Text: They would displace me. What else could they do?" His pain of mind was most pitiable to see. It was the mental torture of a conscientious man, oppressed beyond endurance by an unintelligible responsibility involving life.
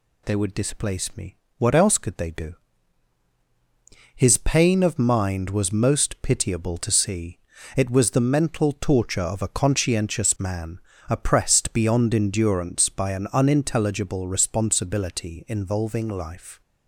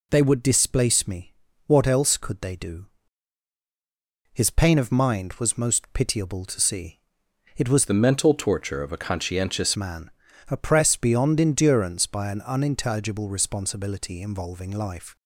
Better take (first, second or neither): first